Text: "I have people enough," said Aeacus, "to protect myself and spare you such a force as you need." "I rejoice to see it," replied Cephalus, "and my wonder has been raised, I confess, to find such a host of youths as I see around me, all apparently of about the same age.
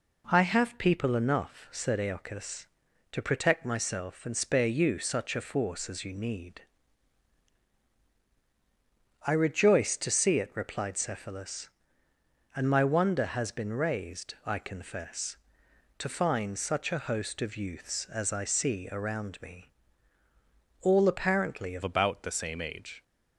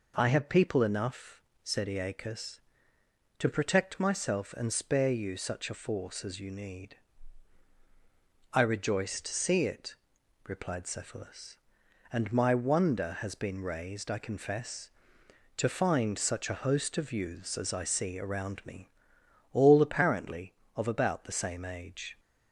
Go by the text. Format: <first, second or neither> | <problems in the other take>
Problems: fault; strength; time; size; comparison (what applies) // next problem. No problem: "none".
second | changes voice at "about"; from 21.8 s on; 1.2 s long